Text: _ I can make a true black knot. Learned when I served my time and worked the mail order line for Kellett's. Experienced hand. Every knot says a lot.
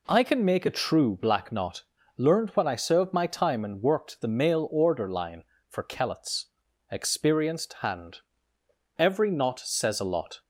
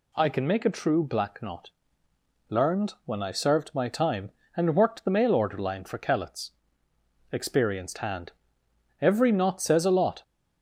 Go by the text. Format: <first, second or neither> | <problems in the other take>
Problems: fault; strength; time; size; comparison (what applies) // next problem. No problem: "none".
neither | none